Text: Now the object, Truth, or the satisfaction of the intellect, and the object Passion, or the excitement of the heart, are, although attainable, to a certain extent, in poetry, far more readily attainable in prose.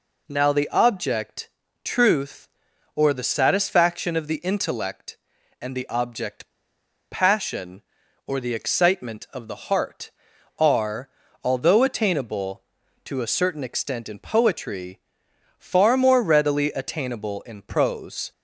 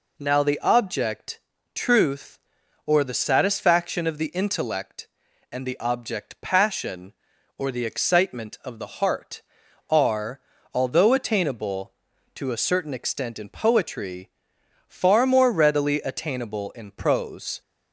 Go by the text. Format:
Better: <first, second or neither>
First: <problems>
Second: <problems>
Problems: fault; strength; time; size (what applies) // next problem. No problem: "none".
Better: second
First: pauses between "object" and "Passion"; noticeable; at 6.4 s; 0.60 s long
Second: none